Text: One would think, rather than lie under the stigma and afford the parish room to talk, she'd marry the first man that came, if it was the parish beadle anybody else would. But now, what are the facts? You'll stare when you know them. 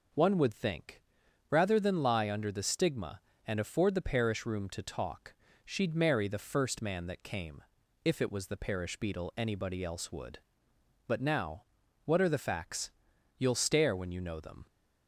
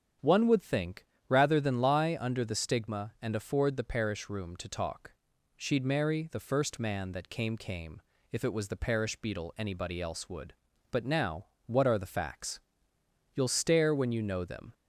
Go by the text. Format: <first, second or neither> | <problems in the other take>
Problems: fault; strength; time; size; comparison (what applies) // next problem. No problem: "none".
first | starts louder than the rest; strong; until 1.4 s; 8 dB // says "came" twice; at 7.5 s